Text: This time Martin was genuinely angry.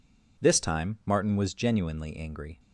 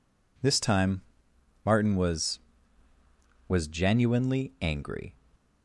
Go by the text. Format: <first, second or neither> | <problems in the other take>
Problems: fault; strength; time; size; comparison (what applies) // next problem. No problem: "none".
first | pauses between "time" and "Martin"; noticeable; at 1.0 s; 0.64 s long // says "was" twice; at 3.4 s